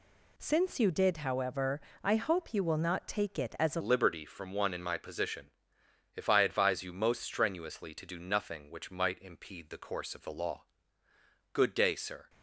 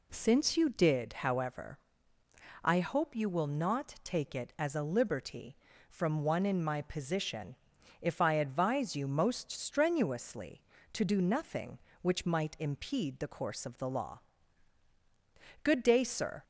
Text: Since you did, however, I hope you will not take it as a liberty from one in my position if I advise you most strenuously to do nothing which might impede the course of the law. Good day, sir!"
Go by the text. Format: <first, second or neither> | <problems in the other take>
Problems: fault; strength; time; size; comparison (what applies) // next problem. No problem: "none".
second | changes voice at "liberty"; from 3.7 s on; 8.5 s long // pauses between "position" and "if"; noticeable; at 5.4 s; 0.66 s long; noticeable in the second